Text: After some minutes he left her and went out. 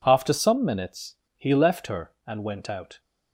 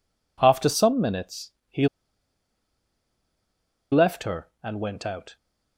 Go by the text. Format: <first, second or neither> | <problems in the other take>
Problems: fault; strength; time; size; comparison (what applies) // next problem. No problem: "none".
first | pauses between "minutes" and "he"; slight; at 1.5 s; 0.18 s long; slight in the first // pauses between "he" and "left"; strong; at 1.8 s; 2.0 s long